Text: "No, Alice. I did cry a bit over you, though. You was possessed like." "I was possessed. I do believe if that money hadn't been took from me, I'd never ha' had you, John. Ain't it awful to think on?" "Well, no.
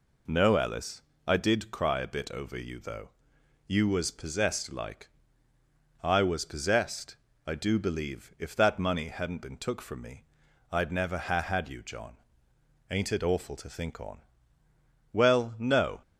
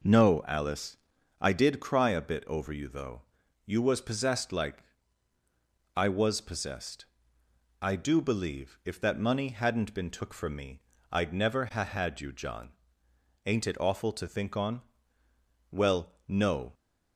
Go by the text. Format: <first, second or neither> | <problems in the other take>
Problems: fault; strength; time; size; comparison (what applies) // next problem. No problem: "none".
neither | none